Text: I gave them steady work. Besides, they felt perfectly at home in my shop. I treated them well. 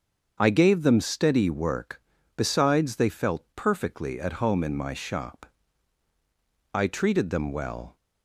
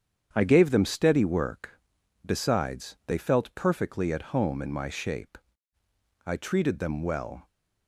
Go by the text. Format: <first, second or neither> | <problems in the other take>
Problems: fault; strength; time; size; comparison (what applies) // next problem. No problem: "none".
first | starts louder than the rest; strong; until 1.3 s; 8.5 dB; also in the first // says "shape" for "shop"; at 4.8 s